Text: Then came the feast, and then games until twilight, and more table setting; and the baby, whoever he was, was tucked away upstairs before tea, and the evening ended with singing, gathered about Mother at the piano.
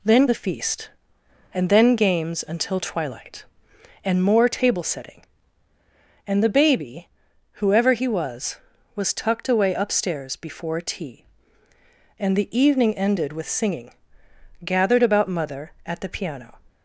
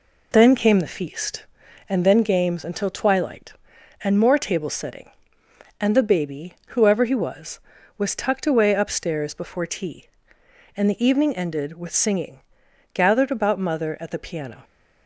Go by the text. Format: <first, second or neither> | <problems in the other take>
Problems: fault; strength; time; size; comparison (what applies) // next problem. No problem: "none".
second | skips "came"; at 0.2 s